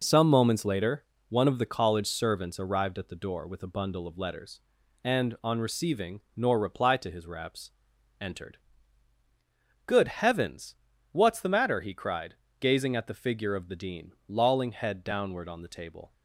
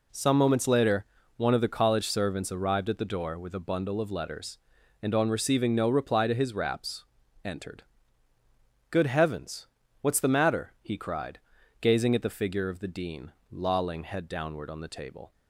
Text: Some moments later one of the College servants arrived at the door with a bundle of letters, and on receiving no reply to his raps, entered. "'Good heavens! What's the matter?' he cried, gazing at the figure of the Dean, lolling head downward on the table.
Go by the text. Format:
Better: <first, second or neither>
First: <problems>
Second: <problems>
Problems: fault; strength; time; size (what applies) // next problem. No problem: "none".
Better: second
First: pauses between "later" and "one"; slight; at 1.0 s; 0.24 s long // says "nor" for "no"; at 6.3 s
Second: pauses between "later" and "one"; slight; at 1.0 s; 0.32 s long